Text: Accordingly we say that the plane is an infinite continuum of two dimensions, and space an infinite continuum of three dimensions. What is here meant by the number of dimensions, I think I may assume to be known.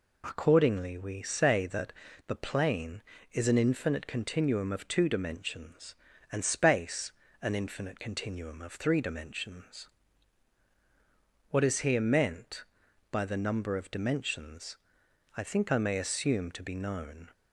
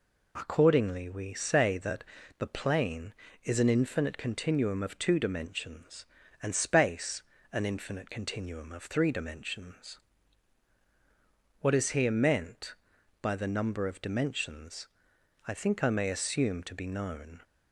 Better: neither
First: pauses between "that" and "the"; slight; at 1.9 s; 0.34 s long // pauses between "space" and "an"; slight; at 7.1 s; 0.32 s long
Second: pauses between "that" and "the"; slight; at 2.0 s; 0.34 s long // pauses between "space" and "an"; slight; at 7.2 s; 0.32 s long

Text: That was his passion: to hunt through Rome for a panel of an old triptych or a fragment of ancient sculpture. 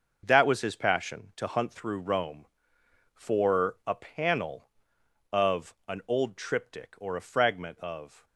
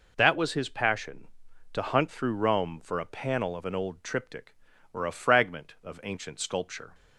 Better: second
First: stops before "ancient sculpture"; at 8.2 s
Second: none

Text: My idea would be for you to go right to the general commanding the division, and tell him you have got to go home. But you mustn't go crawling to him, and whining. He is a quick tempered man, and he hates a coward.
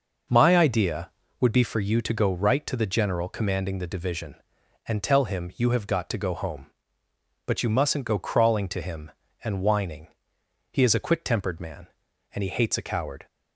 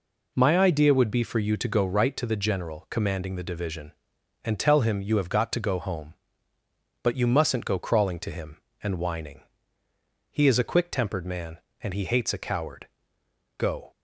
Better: first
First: none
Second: goes on to say "Go"; slight; from 13.5 s on; 0.34 s long

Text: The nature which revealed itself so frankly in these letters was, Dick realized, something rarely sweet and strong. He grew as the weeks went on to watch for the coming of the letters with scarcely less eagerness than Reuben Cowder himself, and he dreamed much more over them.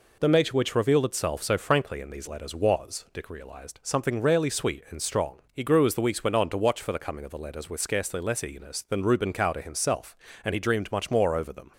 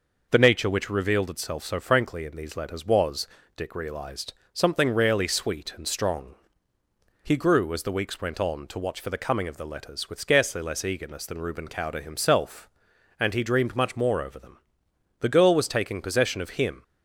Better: first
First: none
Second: goes on to say "The girl was taking possession of him"; from 15.2 s on; 1.6 s long

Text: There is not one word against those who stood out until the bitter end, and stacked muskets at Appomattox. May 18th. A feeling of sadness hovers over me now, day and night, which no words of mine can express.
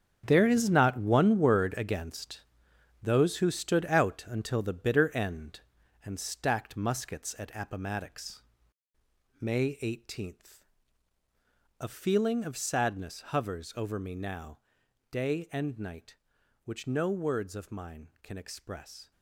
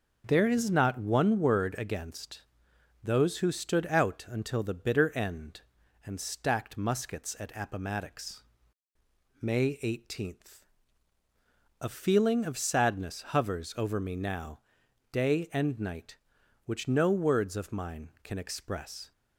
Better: second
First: gets quieter; strong; throughout; 12 dB // starts louder than the rest; strong; until 1.2 s; 8 dB // pauses between "against" and "those"; noticeable; at 2.4 s; 0.62 s long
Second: starts louder than the rest; until 1.2 s; 6 dB // pauses between "against" and "those"; noticeable; at 2.4 s; 0.62 s long

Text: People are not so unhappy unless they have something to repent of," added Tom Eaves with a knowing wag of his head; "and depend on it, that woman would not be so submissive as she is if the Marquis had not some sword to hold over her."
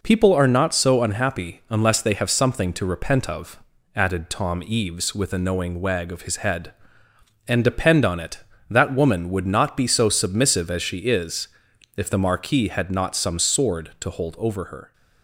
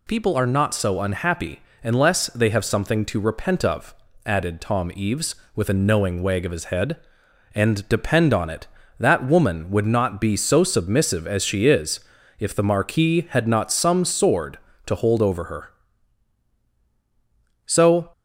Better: first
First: pauses between "is" and "if"; noticeable; at 11.4 s; 0.48 s long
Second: pauses between "unhappy" and "unless"; slight; at 1.5 s; 0.24 s long // pauses between "is" and "if"; at 11.9 s; 0.40 s long // goes on to say "So"; slight; from 17.6 s on; 0.44 s long

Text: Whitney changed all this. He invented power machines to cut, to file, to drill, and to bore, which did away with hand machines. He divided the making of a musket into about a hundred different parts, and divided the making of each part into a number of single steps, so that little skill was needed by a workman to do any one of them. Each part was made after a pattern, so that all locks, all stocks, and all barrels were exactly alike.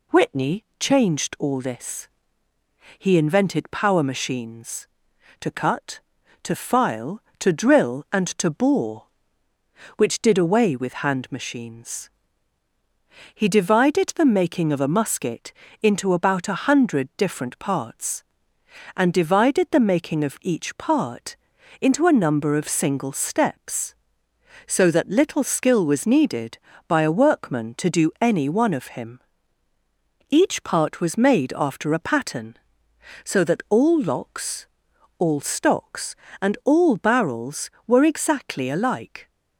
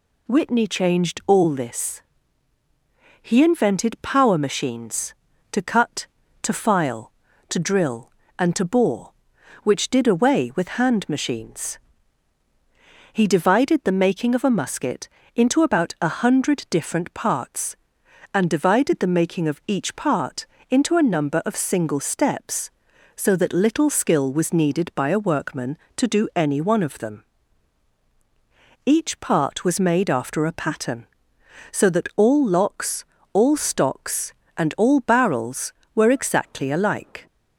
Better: second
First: pauses between "musket" and "into"; slight; at 15.5 s; 0.30 s long // pauses between "part" and "into"; noticeable; at 21.3 s; 0.46 s long // says "him" for "them"; at 28.9 s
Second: pauses between "musket" and "into"; slight; at 15.0 s; 0.28 s long // pauses between "part" and "into"; slight; at 20.4 s; 0.24 s long

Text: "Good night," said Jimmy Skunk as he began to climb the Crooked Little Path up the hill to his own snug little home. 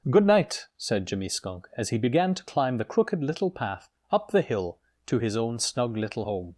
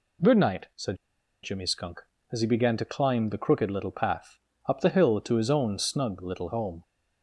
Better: first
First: pauses between "Path" and "up"; slight; at 3.8 s; 0.22 s long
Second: pauses between "said" and "Jimmy"; noticeable; at 0.9 s; 0.47 s long // pauses between "Path" and "up"; slight; at 4.4 s; 0.28 s long

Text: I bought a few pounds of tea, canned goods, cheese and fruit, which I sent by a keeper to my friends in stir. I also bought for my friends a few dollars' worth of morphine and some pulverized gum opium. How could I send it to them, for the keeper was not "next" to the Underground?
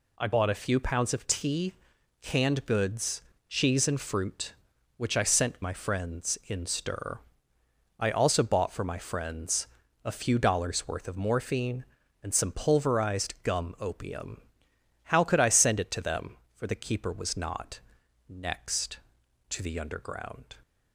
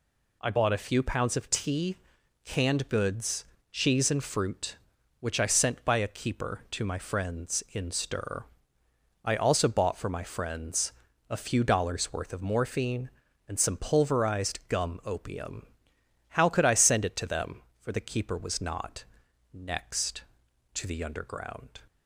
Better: second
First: skips "by a keeper to"; at 5.6 s // pauses between "friends" and "a"; at 9.6 s; 0.38 s long // pauses between "not" and "next"; noticeable; at 17.8 s; 0.48 s long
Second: pauses between "friends" and "a"; at 10.9 s; 0.38 s long // pauses between "not" and "next"; noticeable; at 19.0 s; 0.48 s long

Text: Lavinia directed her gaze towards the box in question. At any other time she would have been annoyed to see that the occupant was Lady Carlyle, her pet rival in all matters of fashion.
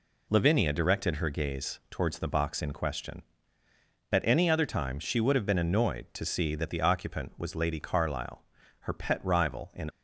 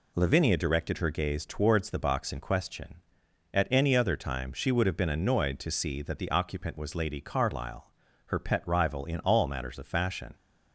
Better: second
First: stops before "all matters of fashion"; at 9.8 s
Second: none

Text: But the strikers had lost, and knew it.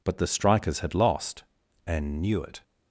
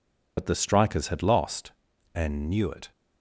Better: first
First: none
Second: loses the start of "But"; at 0.3 s; 45 ms

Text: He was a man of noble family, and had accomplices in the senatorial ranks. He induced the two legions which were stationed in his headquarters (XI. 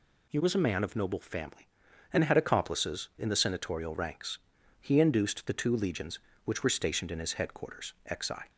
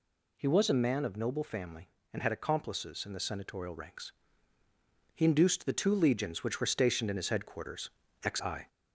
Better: first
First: none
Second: gets louder; slight; throughout; 2 dB

